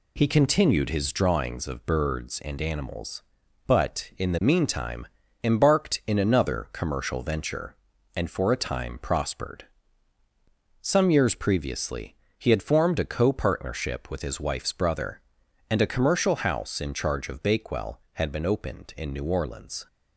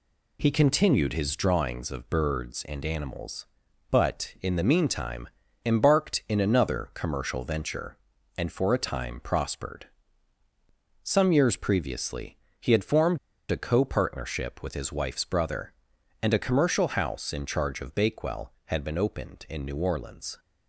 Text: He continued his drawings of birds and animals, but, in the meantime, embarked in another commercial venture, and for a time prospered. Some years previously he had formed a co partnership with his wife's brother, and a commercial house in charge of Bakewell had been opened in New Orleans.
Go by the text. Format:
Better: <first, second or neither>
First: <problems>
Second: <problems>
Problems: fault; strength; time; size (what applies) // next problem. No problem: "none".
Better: first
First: pauses between "previously" and "he"; slight; at 12.1 s; 0.20 s long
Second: pauses between "previously" and "he"; slight; at 12.3 s; 0.20 s long // pauses between "formed" and "a"; slight; at 13.1 s; 0.32 s long